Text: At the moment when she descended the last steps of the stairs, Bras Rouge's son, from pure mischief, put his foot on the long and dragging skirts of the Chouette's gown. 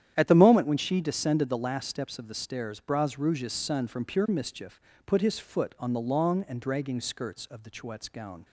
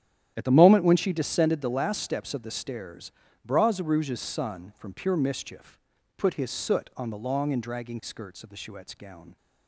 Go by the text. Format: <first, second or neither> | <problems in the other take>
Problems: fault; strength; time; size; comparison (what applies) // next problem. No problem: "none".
first | starts louder than the rest; strong; until 1.3 s; 11 dB; strong in the first // says "soot" for "foot"; at 6.5 s